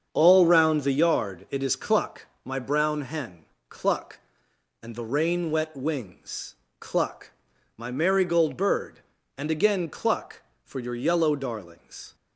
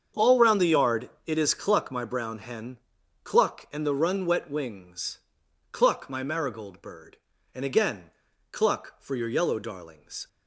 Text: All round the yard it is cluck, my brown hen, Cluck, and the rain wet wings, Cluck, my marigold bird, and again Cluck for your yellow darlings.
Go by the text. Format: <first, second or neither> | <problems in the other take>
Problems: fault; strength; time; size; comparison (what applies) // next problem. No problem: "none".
first | starts louder than the rest; strong; until 1.3 s; 7.5 dB; also in the first // pauses between "yard" and "it"; slight; at 1.0 s; 0.18 s long // says "run" for "rain"; at 3.9 s // pauses between "again" and "Cluck"; at 8.0 s; 0.42 s long